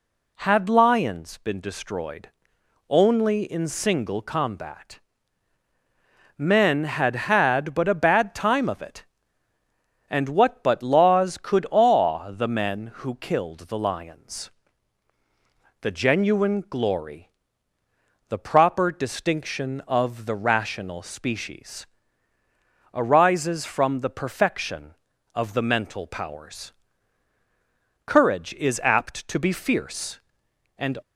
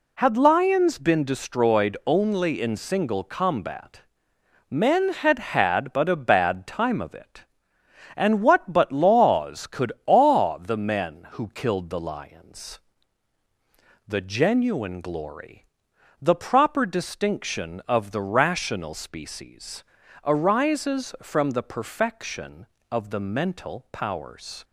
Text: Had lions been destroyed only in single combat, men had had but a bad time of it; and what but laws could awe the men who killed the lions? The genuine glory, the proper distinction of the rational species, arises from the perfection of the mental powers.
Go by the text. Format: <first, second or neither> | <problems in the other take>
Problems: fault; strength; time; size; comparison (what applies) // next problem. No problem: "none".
second | pauses between "destroyed" and "only"; noticeable; at 2.2 s; 0.58 s long // goes on to say "Courage is apt to be fierce and"; strong; from 28.0 s on; 2.9 s long